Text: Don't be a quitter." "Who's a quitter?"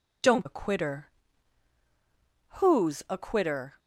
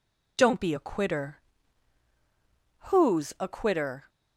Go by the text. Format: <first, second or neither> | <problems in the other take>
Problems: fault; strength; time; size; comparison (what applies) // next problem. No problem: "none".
second | skips "be"; at 0.4 s